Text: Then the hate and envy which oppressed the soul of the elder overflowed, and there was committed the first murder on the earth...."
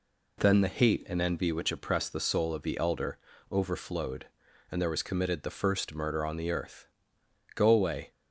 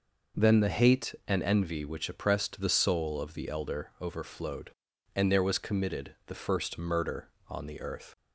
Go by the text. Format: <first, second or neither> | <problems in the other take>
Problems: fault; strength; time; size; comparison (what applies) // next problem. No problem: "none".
second | pauses between "elder" and "overflowed"; slight; at 3.1 s; 0.34 s long // goes on to say "Go away"; from 7.5 s on; 0.54 s long